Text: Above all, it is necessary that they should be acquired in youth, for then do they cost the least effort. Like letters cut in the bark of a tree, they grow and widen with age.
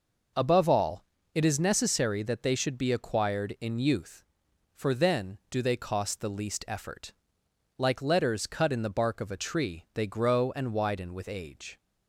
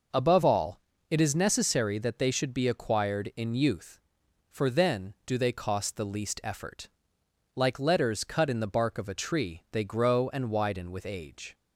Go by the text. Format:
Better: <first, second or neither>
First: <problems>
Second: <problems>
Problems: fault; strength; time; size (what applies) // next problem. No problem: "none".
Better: neither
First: none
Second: none